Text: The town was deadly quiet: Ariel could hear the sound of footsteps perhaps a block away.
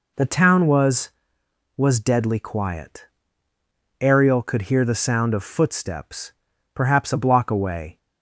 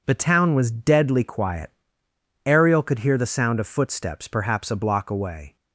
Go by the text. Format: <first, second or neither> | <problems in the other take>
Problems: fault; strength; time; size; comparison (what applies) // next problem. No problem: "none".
second | says "was" twice; at 1.7 s // pauses between "footsteps" and "perhaps"; at 6.3 s; 0.42 s long